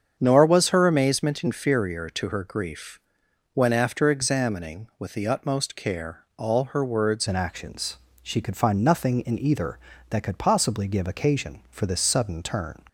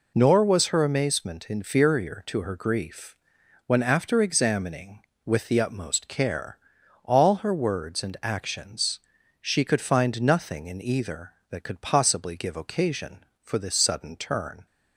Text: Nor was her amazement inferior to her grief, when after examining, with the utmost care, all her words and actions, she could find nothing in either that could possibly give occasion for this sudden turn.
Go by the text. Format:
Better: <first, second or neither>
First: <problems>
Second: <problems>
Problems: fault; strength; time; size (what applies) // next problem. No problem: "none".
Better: second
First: starts louder than the rest; strong; until 1.2 s; 7.5 dB // changes voice at "and"; from 7.2 s on; 5.5 s long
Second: none